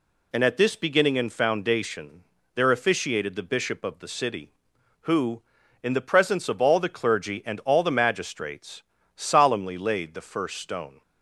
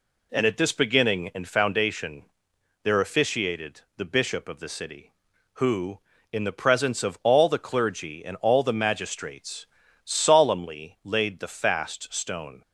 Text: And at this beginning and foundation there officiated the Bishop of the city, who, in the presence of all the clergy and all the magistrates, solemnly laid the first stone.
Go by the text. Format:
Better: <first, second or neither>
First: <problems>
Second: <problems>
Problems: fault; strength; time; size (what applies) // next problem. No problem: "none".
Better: first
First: pauses between "foundation" and "there"; slight; at 2.2 s; 0.32 s long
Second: pauses between "foundation" and "there"; noticeable; at 2.2 s; 0.60 s long // pauses between "officiated" and "the"; slight; at 3.8 s; 0.16 s long // says "fast" for "first"; at 11.4 s